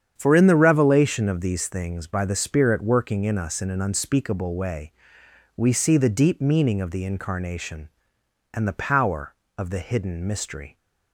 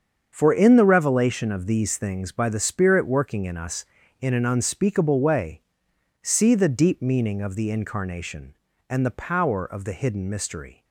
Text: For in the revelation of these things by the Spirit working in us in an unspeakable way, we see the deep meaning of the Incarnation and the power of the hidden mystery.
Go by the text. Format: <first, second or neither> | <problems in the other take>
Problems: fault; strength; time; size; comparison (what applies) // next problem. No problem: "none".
first | starts louder than the rest; strong; until 1.3 s; 7 dB; strong in the first // skips "we"; at 5.9 s